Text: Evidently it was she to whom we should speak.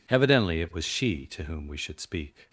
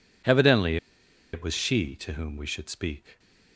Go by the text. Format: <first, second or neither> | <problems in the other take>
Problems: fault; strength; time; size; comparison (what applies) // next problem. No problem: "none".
first | pauses between "Evidently" and "it"; noticeable; at 0.7 s; 0.56 s long